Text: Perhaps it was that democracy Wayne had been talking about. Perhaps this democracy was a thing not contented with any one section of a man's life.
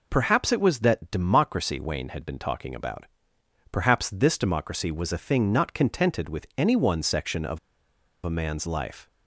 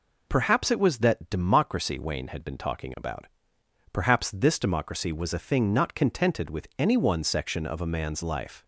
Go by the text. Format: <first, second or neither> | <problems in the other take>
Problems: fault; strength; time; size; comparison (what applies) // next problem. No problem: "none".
second | pauses between "of" and "a"; noticeable; at 7.5 s; 0.66 s long